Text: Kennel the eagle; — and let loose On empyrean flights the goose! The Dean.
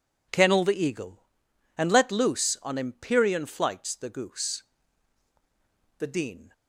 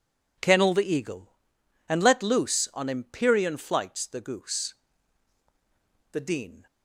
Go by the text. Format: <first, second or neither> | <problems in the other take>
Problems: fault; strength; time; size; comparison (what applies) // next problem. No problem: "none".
neither | none